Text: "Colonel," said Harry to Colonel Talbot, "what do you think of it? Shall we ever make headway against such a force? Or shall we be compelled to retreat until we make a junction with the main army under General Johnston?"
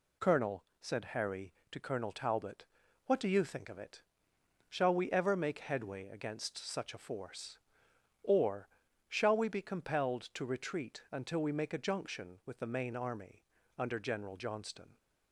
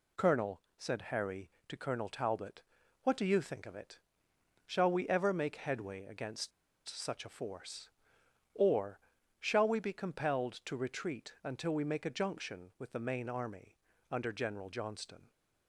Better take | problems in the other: first | pauses between "against" and "such"; at 6.5 s; 0.37 s long // pauses between "Or" and "shall"; at 8.9 s; 0.40 s long; also in the first // pauses between "army" and "under"; slight; at 13.7 s; 0.36 s long; slight in the first

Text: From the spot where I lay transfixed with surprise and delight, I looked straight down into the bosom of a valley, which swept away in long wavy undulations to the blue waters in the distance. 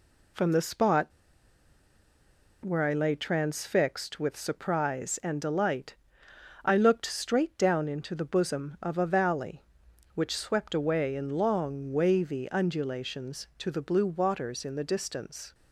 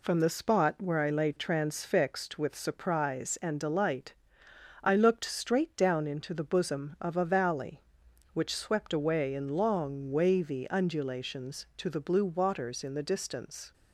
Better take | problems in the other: second | pauses between "spot" and "where"; strong; at 1.1 s; 1.5 s long

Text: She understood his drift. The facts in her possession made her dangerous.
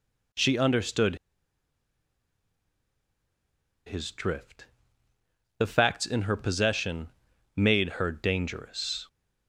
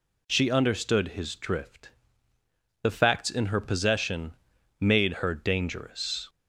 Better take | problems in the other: second | pauses between "understood" and "his"; strong; at 1.1 s; 2.7 s long // pauses between "possession" and "made"; noticeable; at 7.0 s; 0.48 s long; noticeable in the second

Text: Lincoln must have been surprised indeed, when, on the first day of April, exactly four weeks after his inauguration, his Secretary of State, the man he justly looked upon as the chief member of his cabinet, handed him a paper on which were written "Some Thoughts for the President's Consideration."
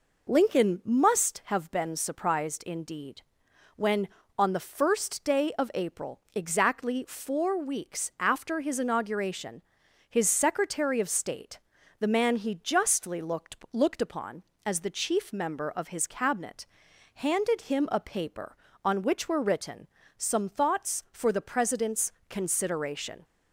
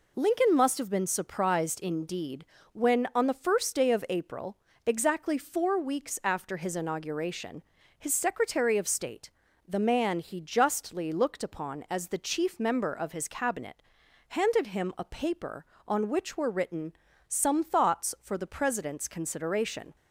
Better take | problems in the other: second | says "looked" twice; at 13.7 s // pauses between "written" and "Some"; slight; at 19.8 s; 0.30 s long; slight in the second // pauses between "President's" and "Consideration"; slight; at 22.1 s; 0.16 s long

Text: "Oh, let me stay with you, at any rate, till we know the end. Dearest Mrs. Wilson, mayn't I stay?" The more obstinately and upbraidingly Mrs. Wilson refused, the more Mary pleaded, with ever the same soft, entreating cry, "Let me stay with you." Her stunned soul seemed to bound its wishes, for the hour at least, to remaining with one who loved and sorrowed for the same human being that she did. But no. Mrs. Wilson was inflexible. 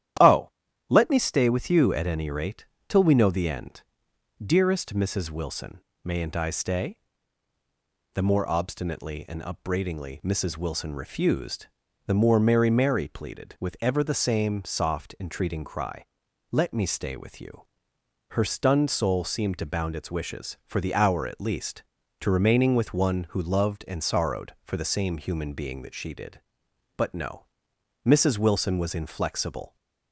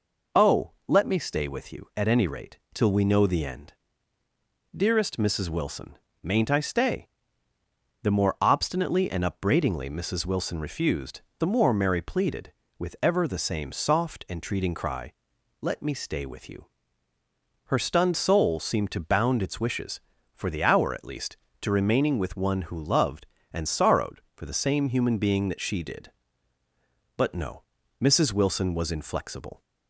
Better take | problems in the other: second | starts louder than the rest; strong; until 1.6 s; 11.5 dB // says "Mary" twice; at 12.7 s

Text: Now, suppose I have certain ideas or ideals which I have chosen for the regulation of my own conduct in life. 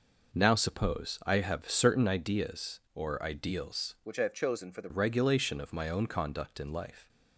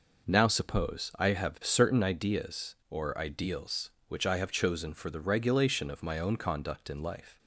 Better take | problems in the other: second | changes voice from "which" to "the"; from 4.0 to 4.8 s; 0.8 s long

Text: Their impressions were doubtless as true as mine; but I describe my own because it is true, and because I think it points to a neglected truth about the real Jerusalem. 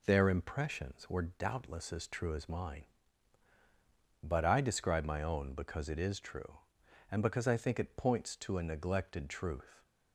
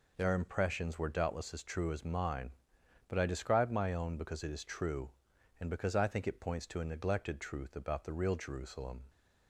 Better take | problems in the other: second | stops before "about the real Jerusalem"; at 9.8 s

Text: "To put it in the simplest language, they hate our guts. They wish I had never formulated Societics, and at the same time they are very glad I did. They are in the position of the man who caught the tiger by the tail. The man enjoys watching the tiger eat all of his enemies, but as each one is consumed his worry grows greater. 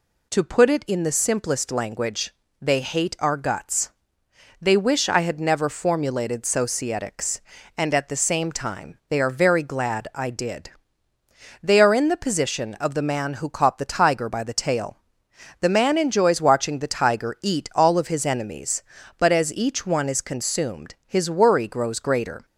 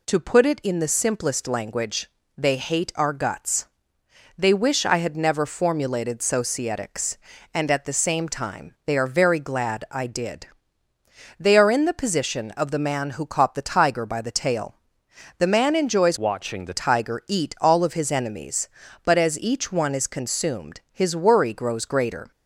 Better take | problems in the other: first | changes voice from "watching" to "the"; from 16.1 to 16.7 s; 0.6 s long

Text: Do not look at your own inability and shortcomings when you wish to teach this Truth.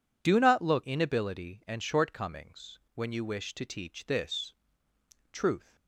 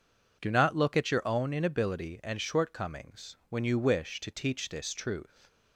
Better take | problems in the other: second | skips "at your own"; at 0.8 s // pauses between "shortcomings" and "when"; slight; at 2.7 s; 0.16 s long // pauses between "this" and "Truth"; noticeable; at 4.5 s; 0.78 s long

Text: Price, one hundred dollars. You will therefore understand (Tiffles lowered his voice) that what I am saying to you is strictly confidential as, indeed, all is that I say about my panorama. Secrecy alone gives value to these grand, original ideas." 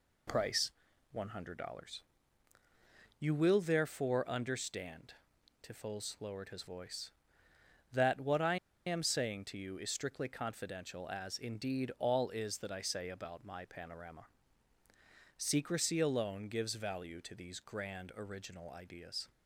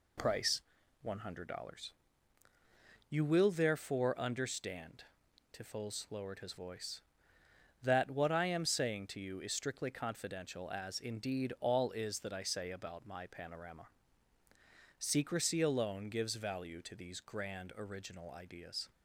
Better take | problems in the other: second | pauses between "I" and "am"; slight; at 8.5 s; 0.29 s long

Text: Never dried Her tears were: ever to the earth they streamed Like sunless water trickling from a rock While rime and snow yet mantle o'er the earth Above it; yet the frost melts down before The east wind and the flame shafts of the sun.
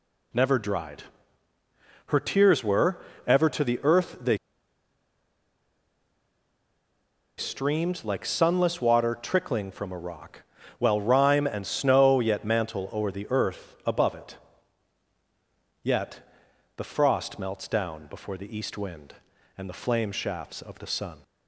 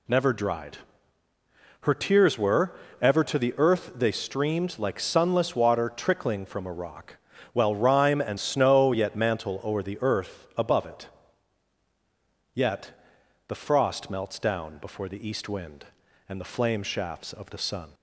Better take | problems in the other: second | pauses between "dried" and "Her"; at 1.0 s; 1.0 s long; also in the second // pauses between "they" and "streamed"; strong; at 4.3 s; 3.0 s long // pauses between "rock" and "While"; at 10.4 s; 0.38 s long; also in the second // pauses between "yet" and "the"; noticeable; at 16.2 s; 0.50 s long; noticeable in the second

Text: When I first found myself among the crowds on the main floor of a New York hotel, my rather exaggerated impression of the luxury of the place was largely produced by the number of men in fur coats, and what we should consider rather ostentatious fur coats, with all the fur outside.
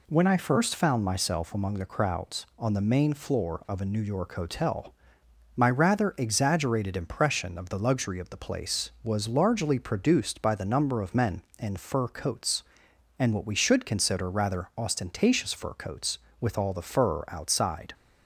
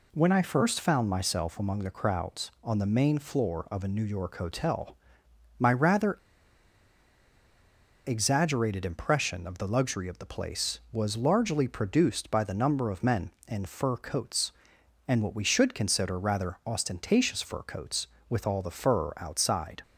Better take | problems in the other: first | pauses between "rather" and "exaggerated"; strong; at 6.1 s; 1.8 s long

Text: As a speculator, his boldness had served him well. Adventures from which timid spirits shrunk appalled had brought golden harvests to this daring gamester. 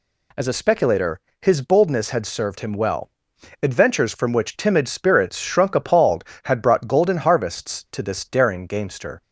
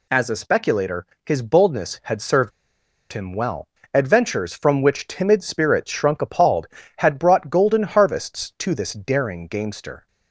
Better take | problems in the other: first | pauses between "served" and "him"; noticeable; at 2.5 s; 0.62 s long

